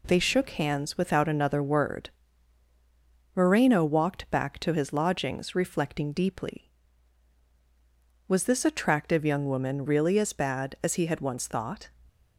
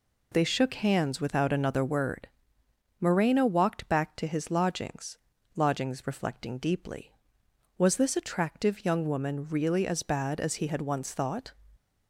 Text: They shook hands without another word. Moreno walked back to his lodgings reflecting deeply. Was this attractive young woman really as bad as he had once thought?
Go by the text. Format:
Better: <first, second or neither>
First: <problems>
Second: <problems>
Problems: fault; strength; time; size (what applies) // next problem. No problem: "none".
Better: first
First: none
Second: says "lodgings" twice; at 5.5 s